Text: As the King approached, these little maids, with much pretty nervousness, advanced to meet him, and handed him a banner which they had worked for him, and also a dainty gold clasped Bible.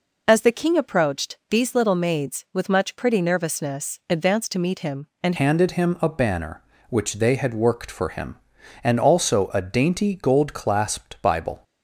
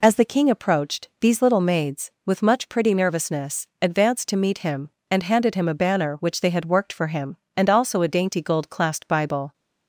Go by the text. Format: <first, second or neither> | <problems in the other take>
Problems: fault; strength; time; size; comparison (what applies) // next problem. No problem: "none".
second | changes voice at "handed"; from 5.3 s on; 6.3 s long